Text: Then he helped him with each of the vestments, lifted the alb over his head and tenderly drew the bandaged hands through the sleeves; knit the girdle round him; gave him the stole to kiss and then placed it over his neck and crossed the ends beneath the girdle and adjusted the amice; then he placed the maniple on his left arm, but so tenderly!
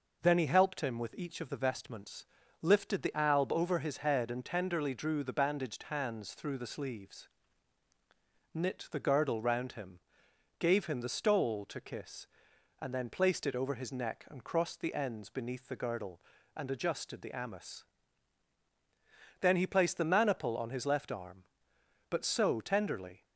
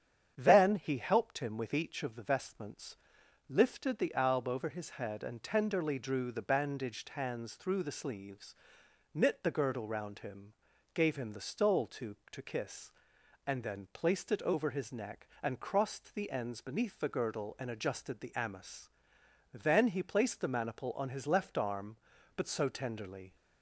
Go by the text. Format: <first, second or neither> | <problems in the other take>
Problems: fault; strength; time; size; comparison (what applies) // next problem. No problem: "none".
first | starts louder than the rest; strong; until 1.3 s; 9 dB // says "to" twice; at 12.3 s